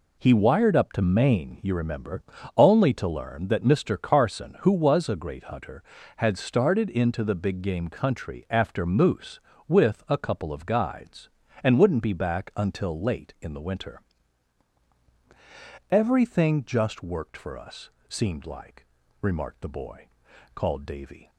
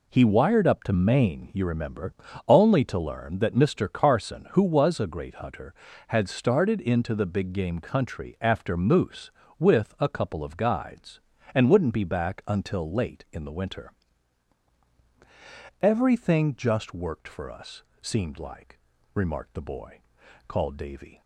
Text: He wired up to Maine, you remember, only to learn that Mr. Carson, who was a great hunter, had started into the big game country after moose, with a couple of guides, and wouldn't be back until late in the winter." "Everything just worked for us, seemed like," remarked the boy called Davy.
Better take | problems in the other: neither | pauses between "boy" and "called"; noticeable; the same in both

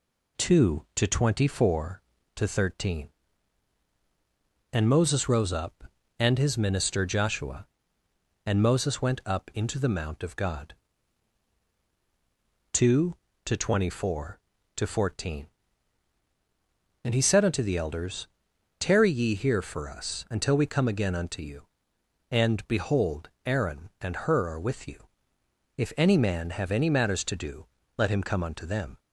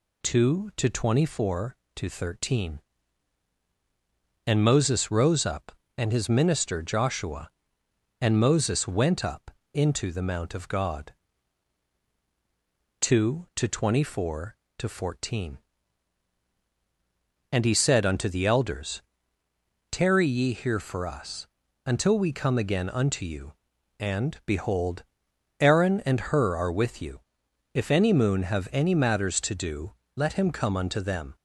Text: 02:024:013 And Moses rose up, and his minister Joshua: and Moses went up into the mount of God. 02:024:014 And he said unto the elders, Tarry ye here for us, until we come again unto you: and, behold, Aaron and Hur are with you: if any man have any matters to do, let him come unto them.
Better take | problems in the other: first | pauses between "up" and "into"; slight; at 9.5 s; 0.22 s long // says "moon" for "man"; at 28.1 s

